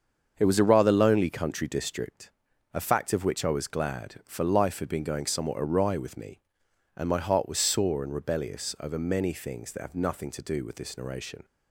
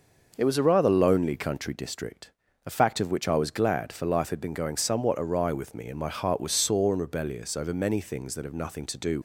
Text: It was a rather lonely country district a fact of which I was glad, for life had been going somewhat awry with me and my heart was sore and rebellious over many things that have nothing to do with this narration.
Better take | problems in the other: first | starts louder than the rest; noticeable; until 1.3 s; 6 dB; also in the first // pauses between "district" and "a"; slight; at 2.2 s; 0.36 s long; also in the first // stops before "with this narration"; at 9.1 s

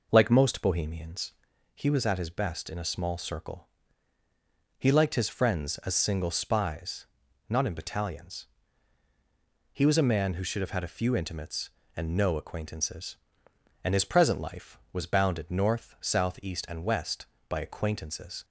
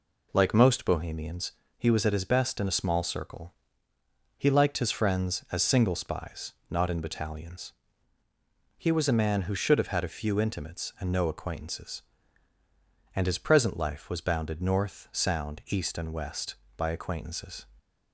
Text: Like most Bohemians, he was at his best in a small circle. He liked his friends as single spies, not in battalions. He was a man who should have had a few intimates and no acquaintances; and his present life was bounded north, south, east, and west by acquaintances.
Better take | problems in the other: first | says "sound" for "south"; at 15.1 s

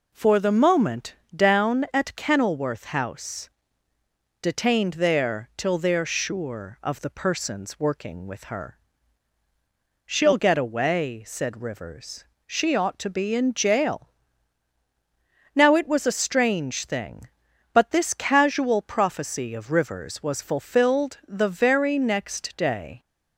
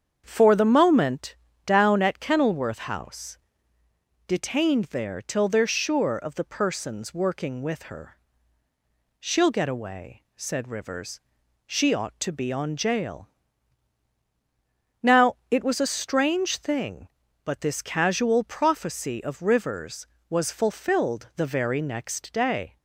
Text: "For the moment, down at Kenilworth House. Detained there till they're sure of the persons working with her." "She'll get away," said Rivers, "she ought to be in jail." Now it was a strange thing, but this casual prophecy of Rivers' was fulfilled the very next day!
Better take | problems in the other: first | starts louder than the rest; strong; until 1.2 s; 7.5 dB // says "on" for "in"; at 12.5 s

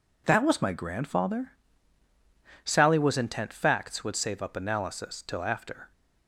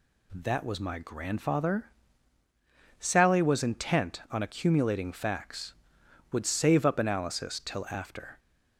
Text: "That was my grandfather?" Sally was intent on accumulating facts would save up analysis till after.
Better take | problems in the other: second | skips "on accumulating"; at 3.5 s

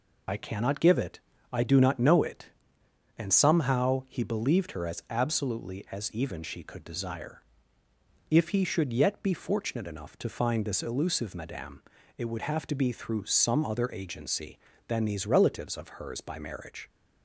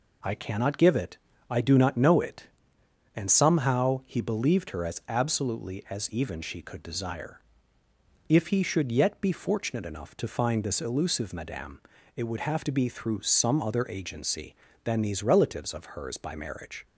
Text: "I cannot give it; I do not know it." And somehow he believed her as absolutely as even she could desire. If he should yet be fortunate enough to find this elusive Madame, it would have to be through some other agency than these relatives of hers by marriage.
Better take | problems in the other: second | loses the start of "I"; at 0.2 s; 30 ms

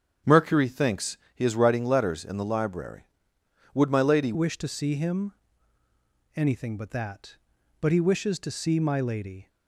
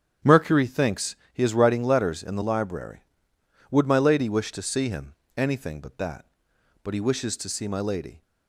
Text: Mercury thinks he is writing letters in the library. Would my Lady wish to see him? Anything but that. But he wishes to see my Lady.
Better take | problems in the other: second | starts louder than the rest; strong; until 1.4 s; 8 dB; strong in the second // pauses between "thinks" and "he"; slight; at 1.1 s; 0.16 s long; slight in the second // changes voice at "wish"; from 4.3 s on; 5.1 s long

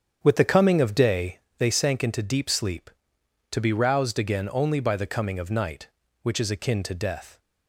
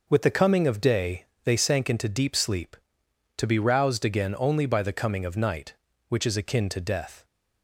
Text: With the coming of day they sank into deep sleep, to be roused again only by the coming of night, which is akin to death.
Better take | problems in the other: second | starts louder than the rest; strong; until 1.4 s; 8 dB // pauses between "day" and "they"; slight; at 1.3 s; 0.18 s long; slight in the second

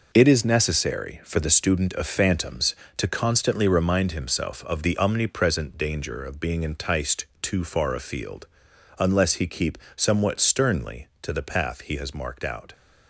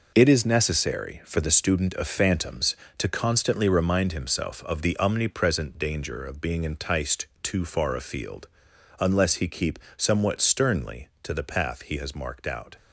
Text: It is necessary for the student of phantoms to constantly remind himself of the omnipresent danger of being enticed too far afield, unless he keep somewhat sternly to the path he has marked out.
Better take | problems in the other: neither | pauses between "keep" and "somewhat"; slight; the same in both

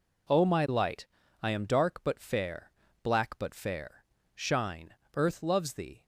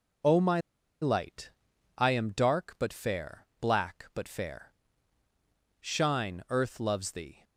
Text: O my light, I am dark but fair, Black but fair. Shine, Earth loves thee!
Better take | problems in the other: first | pauses between "my" and "light"; at 0.6 s; 0.40 s long

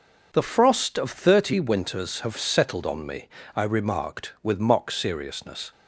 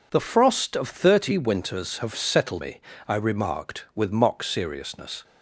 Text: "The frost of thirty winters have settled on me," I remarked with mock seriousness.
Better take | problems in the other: first | skips "on"; at 2.6 s

